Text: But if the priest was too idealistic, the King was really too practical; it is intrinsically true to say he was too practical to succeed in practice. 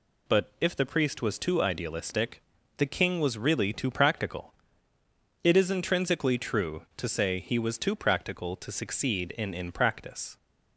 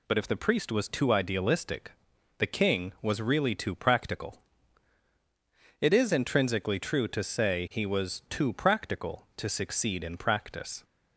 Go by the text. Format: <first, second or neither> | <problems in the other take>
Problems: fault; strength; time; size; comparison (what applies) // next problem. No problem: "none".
second | says "in" twice; at 9.5 s